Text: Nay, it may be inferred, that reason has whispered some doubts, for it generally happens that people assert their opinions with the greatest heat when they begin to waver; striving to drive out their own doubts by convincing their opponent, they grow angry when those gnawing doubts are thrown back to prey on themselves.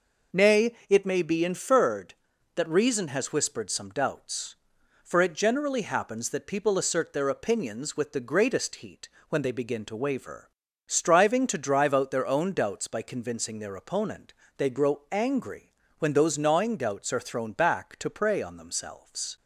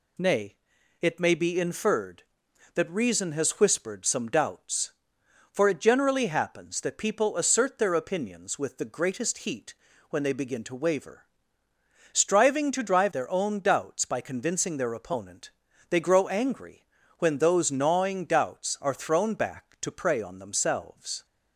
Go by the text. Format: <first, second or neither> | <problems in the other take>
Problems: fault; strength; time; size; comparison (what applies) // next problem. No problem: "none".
first | pauses between "heat" and "when"; slight; at 9.7 s; 0.36 s long; slight in the first // skips "out"; at 13.1 s // pauses between "angry" and "when"; slight; at 16.8 s; 0.32 s long; slight in the first